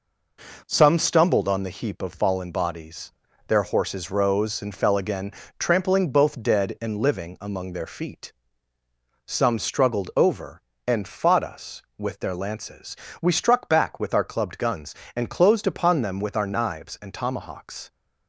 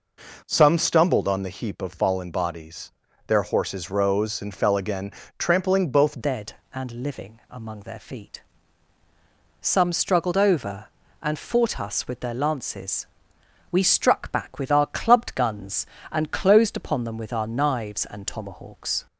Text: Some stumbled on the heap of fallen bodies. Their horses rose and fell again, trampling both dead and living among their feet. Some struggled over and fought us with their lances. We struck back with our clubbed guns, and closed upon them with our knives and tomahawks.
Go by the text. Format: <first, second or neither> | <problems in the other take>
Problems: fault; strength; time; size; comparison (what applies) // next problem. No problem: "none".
first | changes voice at "dead"; from 6.2 s on; 12.8 s long